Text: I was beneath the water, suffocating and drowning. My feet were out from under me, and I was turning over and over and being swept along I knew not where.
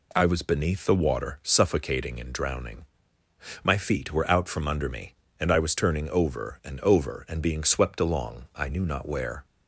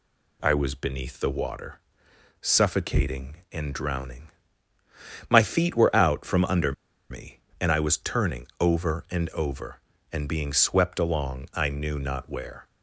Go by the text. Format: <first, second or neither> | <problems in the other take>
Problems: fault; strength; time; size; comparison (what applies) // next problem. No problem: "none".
first | pauses between "under" and "me"; at 6.7 s; 0.37 s long